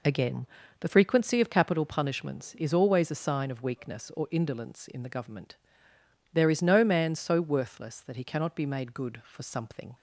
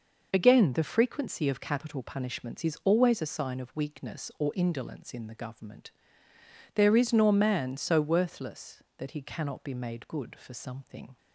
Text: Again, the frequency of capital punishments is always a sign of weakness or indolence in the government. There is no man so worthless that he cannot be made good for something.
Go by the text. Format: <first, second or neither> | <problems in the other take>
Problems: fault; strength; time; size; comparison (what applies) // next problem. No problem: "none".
first | says "nor" for "no"; at 7.1 s